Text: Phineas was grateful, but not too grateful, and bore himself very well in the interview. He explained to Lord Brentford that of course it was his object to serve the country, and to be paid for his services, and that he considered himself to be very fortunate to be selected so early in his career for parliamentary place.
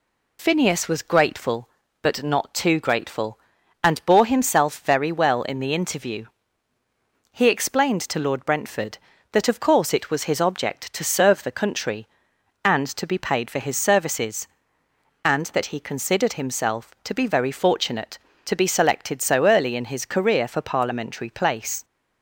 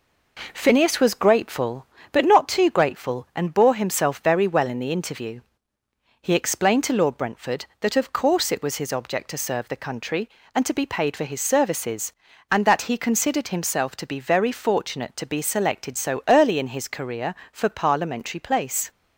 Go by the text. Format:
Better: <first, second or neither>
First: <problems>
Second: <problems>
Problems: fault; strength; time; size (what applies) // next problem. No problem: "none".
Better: neither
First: none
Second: none